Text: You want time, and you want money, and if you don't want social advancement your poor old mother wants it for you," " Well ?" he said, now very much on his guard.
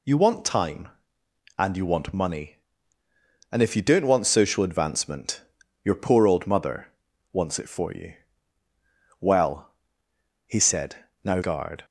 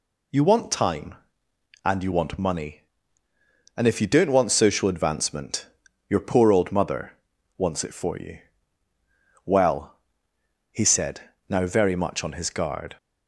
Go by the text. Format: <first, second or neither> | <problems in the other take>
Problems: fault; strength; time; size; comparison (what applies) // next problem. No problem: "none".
second | pauses between "advancement" and "your"; at 5.3 s; 0.42 s long; also in the second // pauses between "mother" and "wants"; at 6.8 s; 0.44 s long; also in the second // skips "very much on his"; at 11.4 s